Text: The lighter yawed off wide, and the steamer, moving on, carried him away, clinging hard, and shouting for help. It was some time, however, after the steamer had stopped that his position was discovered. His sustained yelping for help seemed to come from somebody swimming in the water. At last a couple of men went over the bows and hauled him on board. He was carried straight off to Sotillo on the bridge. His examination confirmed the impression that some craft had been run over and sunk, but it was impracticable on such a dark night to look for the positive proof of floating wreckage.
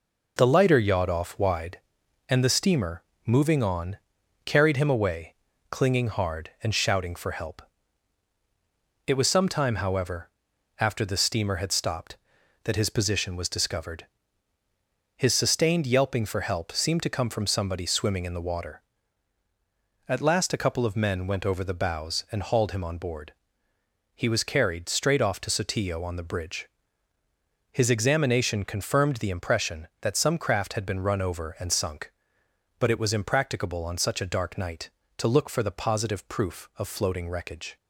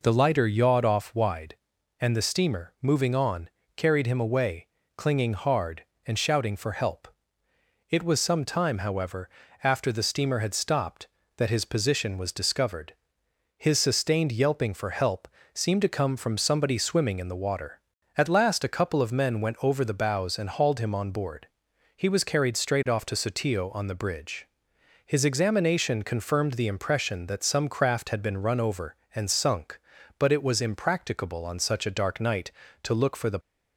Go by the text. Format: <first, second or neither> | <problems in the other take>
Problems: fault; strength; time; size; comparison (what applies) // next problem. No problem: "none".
first | pauses between "help" and "seemed"; slight; at 15.2 s; 0.26 s long // stops before "positive proof of floating wreckage"; at 33.4 s